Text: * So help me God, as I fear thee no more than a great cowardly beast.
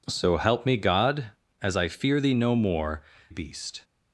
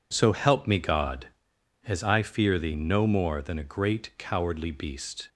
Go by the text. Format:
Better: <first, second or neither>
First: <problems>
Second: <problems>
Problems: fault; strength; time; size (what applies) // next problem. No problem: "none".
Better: second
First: skips "than a great cowardly"; at 3.1 s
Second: none